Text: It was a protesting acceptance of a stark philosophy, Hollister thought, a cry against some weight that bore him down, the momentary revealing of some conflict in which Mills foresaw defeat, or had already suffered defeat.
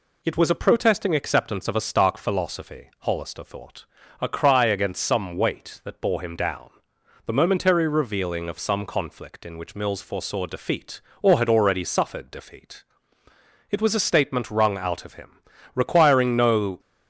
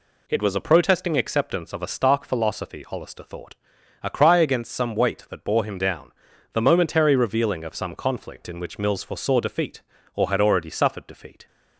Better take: second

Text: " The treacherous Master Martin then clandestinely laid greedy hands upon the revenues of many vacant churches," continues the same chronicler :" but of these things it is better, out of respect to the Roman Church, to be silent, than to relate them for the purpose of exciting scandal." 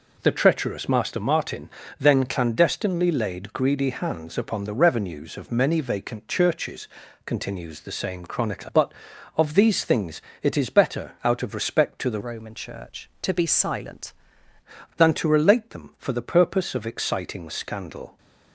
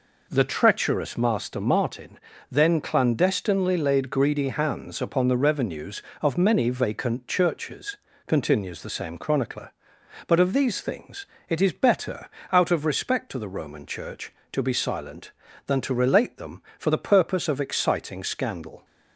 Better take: second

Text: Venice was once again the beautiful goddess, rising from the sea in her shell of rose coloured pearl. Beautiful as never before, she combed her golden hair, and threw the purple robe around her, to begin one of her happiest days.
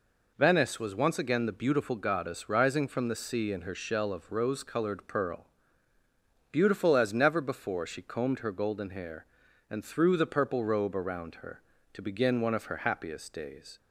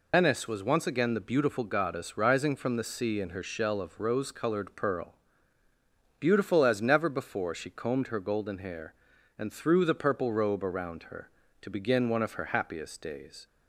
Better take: first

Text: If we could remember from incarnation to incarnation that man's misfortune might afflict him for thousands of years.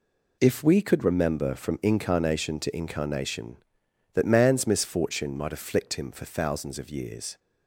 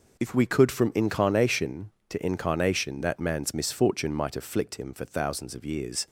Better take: first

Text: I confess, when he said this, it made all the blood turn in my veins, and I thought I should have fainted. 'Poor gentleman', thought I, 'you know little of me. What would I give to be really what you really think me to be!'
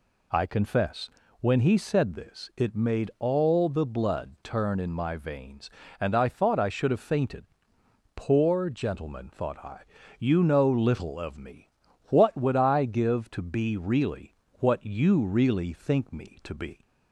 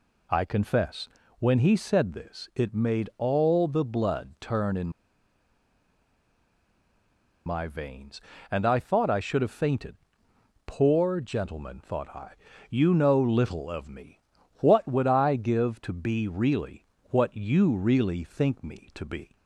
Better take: first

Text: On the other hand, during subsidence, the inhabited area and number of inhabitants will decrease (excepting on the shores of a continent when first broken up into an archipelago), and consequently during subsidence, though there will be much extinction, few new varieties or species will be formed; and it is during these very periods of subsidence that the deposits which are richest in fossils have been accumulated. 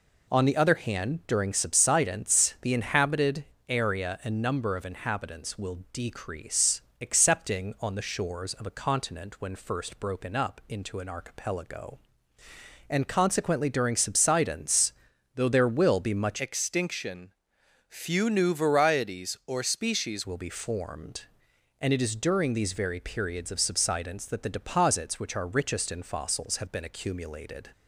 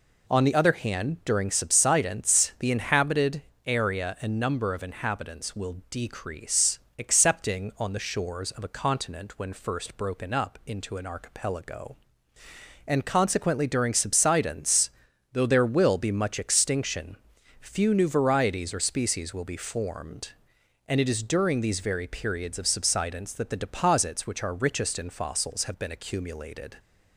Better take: second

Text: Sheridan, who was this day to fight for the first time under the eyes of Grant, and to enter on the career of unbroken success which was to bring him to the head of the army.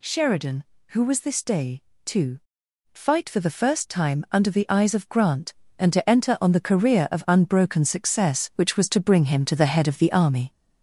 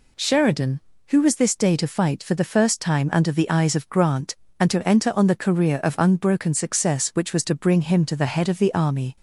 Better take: second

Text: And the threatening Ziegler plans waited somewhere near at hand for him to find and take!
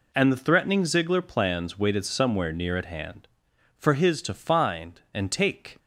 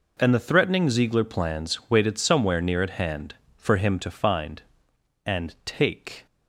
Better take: second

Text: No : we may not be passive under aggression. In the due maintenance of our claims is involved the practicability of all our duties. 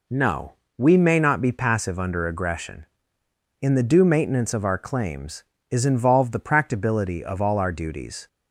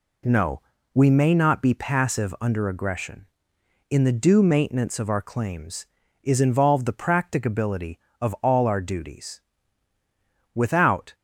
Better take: first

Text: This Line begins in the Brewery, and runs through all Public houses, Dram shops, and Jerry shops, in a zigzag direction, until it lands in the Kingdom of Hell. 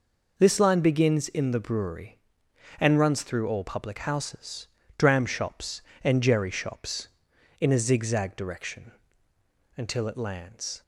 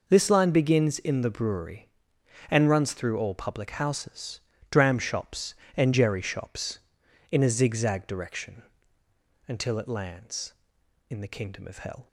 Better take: second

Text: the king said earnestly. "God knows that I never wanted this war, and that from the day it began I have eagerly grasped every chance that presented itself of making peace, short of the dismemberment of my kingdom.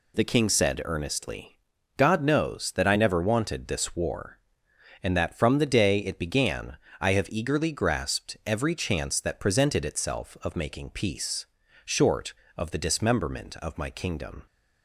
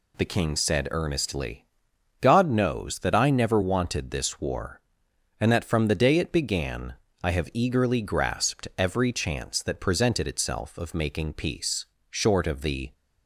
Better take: first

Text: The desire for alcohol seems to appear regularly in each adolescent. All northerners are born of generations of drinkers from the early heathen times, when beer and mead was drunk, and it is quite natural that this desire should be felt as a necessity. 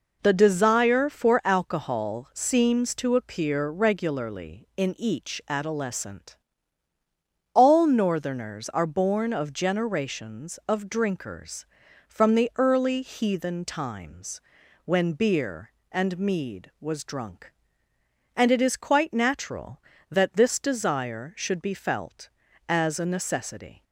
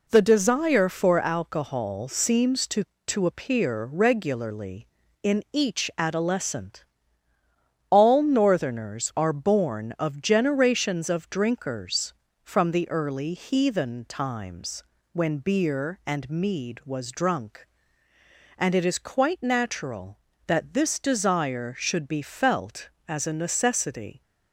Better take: first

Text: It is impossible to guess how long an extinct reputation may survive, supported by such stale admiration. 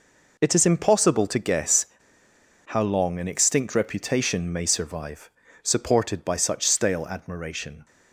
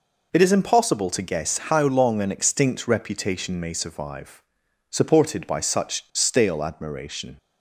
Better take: second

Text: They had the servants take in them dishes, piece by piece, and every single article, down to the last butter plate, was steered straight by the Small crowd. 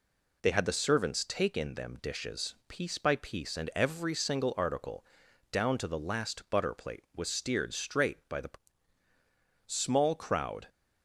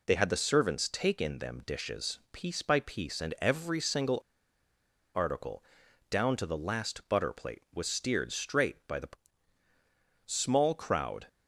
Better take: first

